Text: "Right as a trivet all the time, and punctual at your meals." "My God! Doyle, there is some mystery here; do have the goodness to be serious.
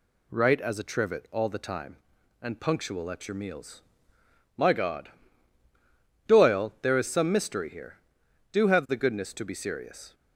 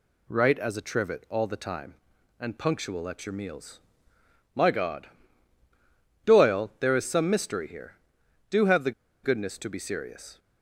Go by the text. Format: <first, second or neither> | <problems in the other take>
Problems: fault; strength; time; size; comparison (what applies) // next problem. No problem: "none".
first | pauses between "the" and "goodness"; slight; at 8.9 s; 0.32 s long